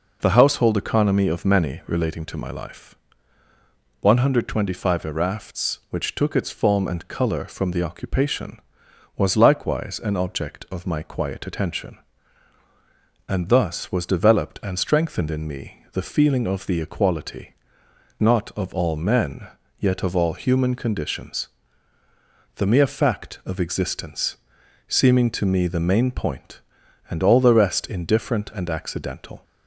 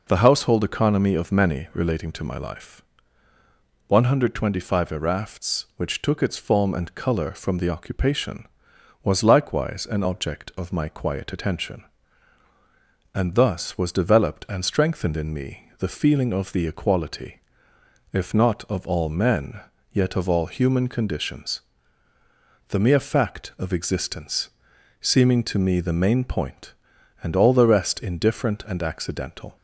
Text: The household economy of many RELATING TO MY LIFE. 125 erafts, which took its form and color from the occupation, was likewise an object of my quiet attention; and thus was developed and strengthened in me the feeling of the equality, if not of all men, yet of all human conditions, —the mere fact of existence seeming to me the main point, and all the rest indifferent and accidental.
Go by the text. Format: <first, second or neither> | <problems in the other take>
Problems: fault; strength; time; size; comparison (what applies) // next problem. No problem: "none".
second | skips "if"; at 17.8 s // pauses between "existence" and "seeming"; noticeable; at 24.3 s; 0.50 s long; noticeable in the second